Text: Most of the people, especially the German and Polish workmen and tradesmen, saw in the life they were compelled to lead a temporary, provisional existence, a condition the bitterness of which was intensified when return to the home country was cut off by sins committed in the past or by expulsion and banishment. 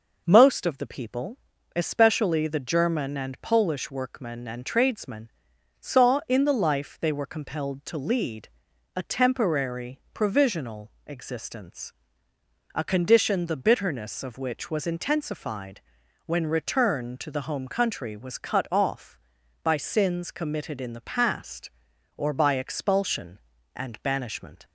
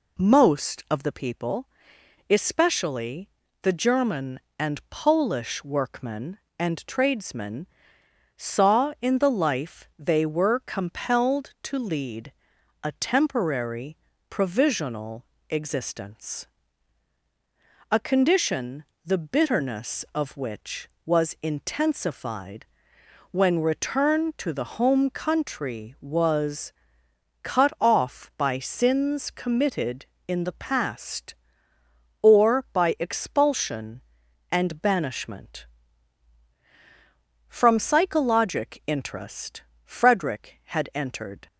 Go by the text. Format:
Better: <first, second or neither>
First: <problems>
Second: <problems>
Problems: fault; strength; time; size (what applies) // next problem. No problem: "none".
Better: first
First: pauses between "lead" and "a"; noticeable; at 8.4 s; 0.48 s long // pauses between "intensified" and "when"; at 15.8 s; 0.44 s long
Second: pauses between "especially" and "the"; slight; at 3.2 s; 0.32 s long // pauses between "lead" and "a"; noticeable; at 12.3 s; 0.50 s long // pauses between "provisional" and "existence"; slight; at 15.2 s; 0.24 s long // pauses between "condition" and "the"; slight; at 18.8 s; 0.20 s long // pauses between "intensified" and "when"; noticeable; at 22.6 s; 0.66 s long // pauses between "was" and "cut"; noticeable; at 26.7 s; 0.70 s long // goes on to say "From psychologic interest Frederick had entered"; strong; from 37.4 s on; 4.0 s long